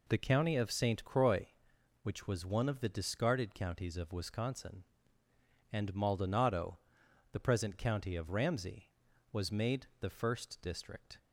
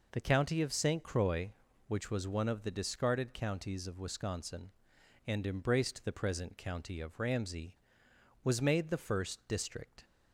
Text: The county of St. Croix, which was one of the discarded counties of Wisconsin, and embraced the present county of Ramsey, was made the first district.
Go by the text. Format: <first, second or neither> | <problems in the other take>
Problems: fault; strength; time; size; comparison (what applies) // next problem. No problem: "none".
second | says "maldonado" for "embraced"; at 5.9 s